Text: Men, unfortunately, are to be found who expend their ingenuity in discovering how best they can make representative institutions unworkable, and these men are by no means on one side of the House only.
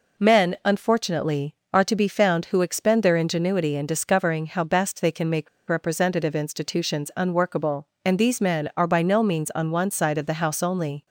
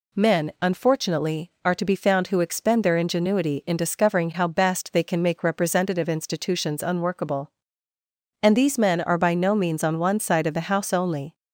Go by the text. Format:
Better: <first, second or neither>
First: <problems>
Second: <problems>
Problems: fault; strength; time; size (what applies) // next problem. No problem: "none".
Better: second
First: pauses between "make" and "representative"; slight; at 5.4 s; 0.20 s long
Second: none